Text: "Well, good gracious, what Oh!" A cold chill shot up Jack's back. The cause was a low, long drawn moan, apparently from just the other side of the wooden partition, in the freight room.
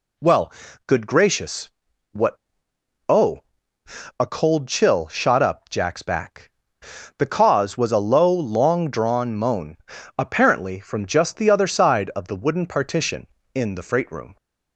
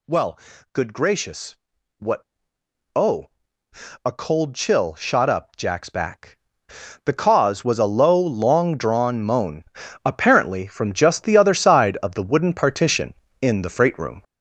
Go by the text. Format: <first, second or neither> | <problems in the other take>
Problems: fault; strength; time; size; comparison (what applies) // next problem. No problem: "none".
first | gets louder; strong; throughout; 7.5 dB // pauses between "what" and "Oh"; noticeable; at 2.2 s; 0.68 s long; noticeable in the first